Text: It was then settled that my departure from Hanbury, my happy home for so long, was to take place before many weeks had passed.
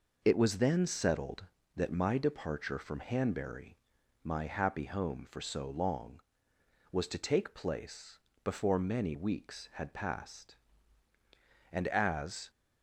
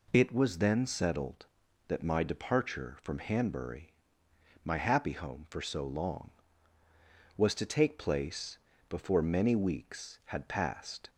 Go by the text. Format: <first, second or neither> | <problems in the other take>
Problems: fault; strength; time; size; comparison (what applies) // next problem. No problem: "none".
second | pauses between "place" and "before"; slight; at 8.1 s; 0.26 s long; slight in the second // goes on to say "And as"; noticeable; from 11.7 s on; 0.78 s long